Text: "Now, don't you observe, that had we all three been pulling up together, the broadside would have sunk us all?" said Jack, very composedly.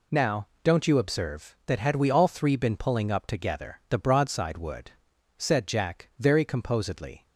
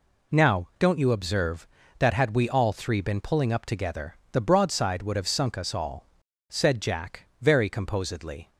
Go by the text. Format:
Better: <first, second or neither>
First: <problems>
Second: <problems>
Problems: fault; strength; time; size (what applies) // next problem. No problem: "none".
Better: second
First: skips "have sunk us all"; at 5.1 s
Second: none